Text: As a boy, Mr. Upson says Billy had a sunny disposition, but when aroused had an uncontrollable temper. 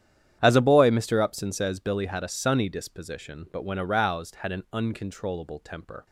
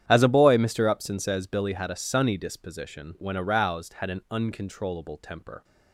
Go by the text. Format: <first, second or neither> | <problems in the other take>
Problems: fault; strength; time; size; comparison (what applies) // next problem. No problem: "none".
first | starts louder than the rest; strong; until 1.0 s; 9.5 dB; strong in the first // skips "but"; at 3.1 s